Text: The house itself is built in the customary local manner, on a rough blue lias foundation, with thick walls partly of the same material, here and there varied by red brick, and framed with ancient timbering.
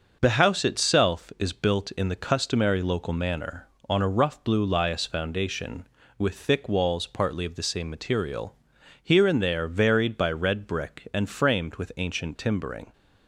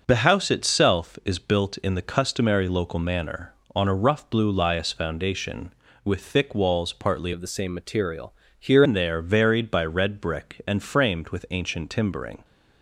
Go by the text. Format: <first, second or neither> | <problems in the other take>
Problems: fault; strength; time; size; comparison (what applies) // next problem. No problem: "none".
first | starts louder than the rest; noticeable; until 1.0 s; 6 dB; also in the first // changes voice from "of" to "here"; from 7.3 to 8.8 s; 1.5 s long